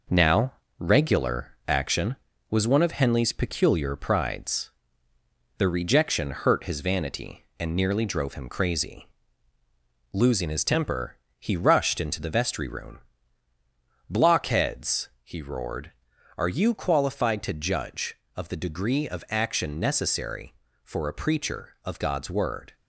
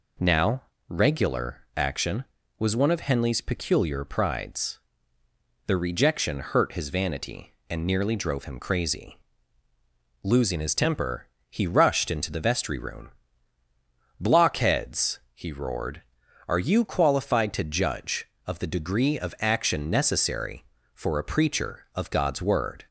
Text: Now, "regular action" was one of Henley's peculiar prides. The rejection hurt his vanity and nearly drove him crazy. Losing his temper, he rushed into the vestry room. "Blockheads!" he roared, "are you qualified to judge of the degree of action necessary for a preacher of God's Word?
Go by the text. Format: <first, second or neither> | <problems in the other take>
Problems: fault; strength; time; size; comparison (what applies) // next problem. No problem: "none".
second | gets quieter; noticeable; throughout; 5 dB